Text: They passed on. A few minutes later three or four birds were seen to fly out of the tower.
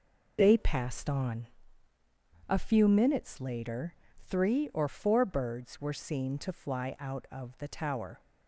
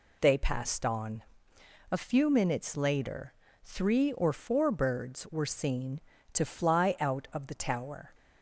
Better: neither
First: pauses between "later" and "three"; slight; at 3.9 s; 0.28 s long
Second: pauses between "later" and "three"; slight; at 3.3 s; 0.32 s long

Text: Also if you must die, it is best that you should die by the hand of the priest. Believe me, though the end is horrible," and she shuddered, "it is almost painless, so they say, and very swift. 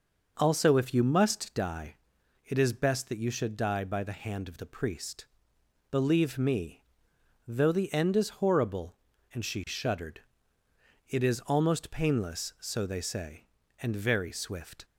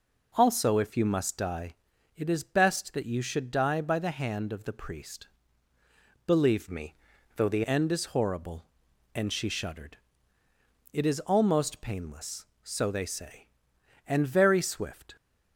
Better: first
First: none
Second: changes voice from "me" to "the"; from 6.7 to 7.6 s; 0.9 s long

